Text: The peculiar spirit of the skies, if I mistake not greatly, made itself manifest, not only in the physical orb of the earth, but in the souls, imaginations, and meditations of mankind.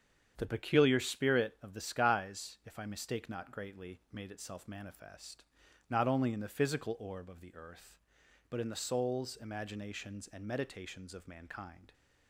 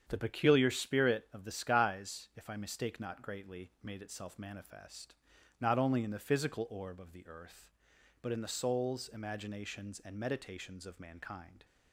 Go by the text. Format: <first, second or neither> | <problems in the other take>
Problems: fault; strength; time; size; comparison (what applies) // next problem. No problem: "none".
neither | starts louder than the rest; strong; the same in both